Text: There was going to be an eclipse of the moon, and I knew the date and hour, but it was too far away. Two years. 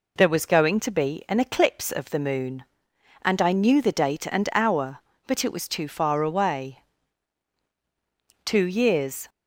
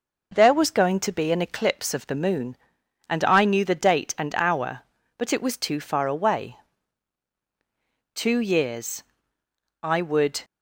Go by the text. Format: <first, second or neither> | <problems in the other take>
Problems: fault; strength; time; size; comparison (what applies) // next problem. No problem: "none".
first | goes on to say "I would"; noticeable; from 9.8 s on; 0.62 s long